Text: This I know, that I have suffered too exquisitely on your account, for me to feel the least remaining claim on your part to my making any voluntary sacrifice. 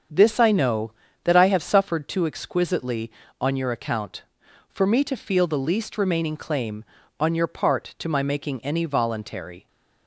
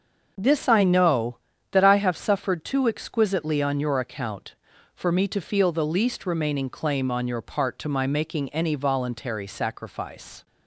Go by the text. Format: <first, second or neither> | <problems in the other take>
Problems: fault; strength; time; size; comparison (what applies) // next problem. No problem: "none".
second | starts louder than the rest; strong; until 1.4 s; 7.5 dB; also in the second // stops before "sacrifice"; at 9.6 s